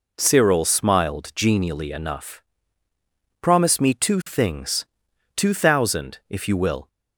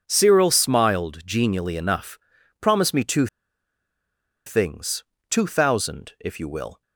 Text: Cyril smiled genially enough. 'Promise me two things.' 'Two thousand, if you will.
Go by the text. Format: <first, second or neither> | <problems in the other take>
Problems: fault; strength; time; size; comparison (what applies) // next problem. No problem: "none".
first | pauses between "two" and "things"; at 3.2 s; 1.2 s long